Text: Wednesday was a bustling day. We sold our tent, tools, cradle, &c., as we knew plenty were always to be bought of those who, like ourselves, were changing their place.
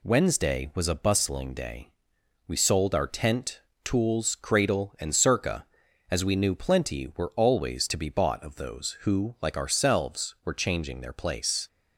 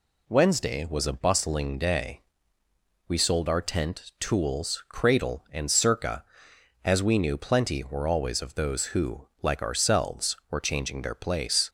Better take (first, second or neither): first